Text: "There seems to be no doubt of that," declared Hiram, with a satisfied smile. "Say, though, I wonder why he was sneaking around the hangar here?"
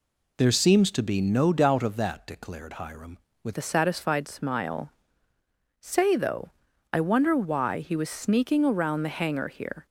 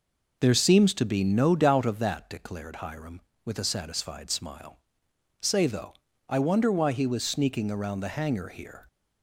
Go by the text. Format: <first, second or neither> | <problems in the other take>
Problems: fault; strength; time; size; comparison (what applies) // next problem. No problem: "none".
second | changes voice at "a"; from 3.5 s on; 6.3 s long